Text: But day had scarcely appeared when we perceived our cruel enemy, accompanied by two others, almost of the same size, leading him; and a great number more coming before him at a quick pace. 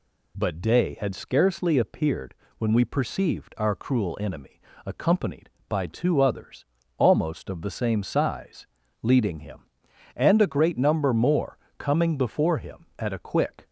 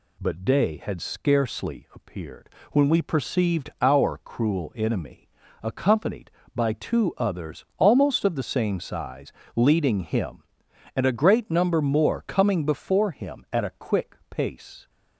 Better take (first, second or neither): second